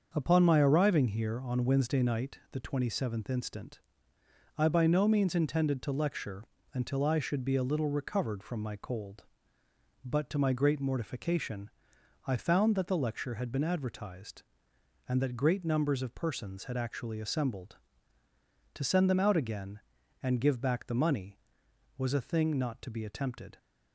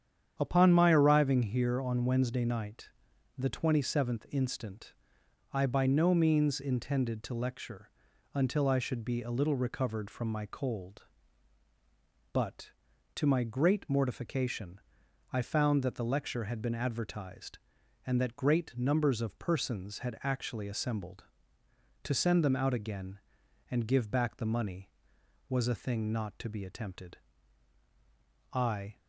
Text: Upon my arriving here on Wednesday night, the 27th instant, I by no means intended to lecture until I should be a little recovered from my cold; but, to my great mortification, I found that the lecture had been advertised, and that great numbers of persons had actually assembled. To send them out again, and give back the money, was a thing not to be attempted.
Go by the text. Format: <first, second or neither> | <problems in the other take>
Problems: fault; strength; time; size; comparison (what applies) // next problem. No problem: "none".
first | starts louder than the rest; strong; until 1.3 s; 8.5 dB; also in the first // pauses between "lecture" and "until"; noticeable; at 7.8 s; 0.46 s long; slight in the first // goes on to say "I"; slight; from 28.5 s on; 0.44 s long